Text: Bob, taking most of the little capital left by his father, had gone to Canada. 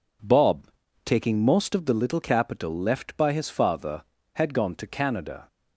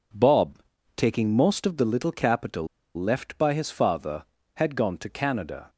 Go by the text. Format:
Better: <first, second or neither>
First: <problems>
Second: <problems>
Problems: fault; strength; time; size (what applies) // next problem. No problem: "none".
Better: first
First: none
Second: pauses between "capital" and "left"; slight; at 2.6 s; 0.30 s long